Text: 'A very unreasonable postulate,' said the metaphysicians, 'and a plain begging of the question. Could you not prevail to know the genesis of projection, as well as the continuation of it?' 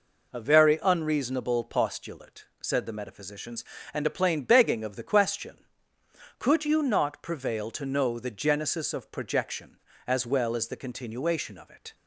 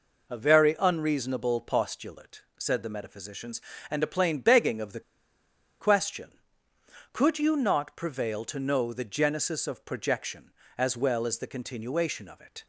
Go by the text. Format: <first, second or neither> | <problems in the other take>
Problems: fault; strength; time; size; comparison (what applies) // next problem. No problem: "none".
first | pauses between "the" and "question"; noticeable; at 4.9 s; 0.79 s long